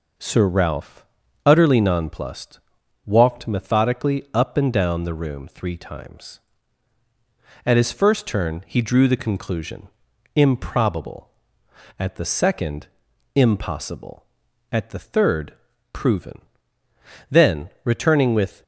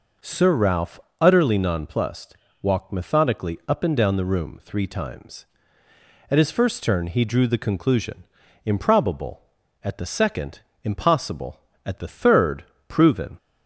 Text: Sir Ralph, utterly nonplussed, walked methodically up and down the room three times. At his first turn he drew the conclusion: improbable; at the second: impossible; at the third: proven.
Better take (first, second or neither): second